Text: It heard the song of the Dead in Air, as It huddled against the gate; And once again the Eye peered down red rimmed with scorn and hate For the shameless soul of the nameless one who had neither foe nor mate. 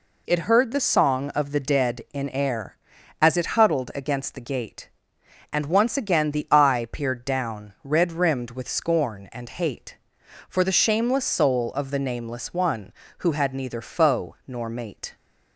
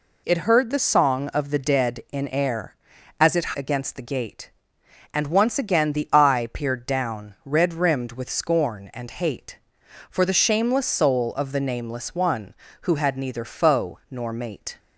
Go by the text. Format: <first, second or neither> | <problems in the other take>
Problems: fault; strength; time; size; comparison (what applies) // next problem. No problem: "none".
first | skips "huddled"; at 3.5 s